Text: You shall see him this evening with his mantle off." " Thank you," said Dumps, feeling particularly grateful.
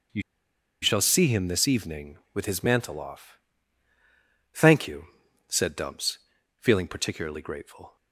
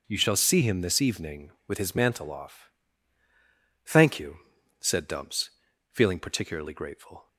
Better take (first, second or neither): second